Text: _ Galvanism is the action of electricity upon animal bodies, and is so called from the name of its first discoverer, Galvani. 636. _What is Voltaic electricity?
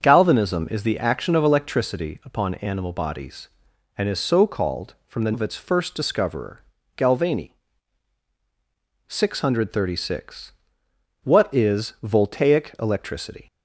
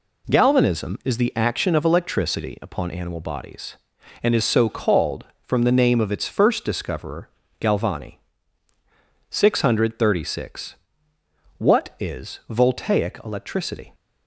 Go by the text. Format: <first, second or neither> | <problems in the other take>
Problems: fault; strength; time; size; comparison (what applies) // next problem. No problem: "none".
second | starts louder than the rest; until 1.0 s; 7 dB // skips "name"; at 5.3 s